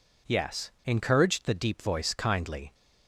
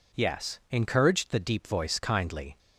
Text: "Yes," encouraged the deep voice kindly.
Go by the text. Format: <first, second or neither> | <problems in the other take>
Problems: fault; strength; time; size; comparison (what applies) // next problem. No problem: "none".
neither | none